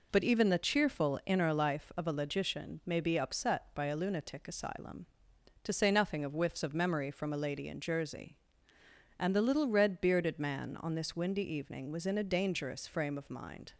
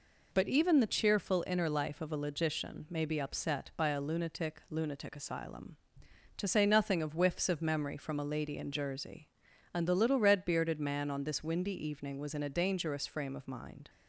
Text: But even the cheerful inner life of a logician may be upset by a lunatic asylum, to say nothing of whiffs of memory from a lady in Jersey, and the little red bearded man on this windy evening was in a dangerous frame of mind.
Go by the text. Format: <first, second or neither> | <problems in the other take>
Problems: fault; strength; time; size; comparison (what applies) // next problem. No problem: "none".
first | says "lunatic" twice; at 4.6 s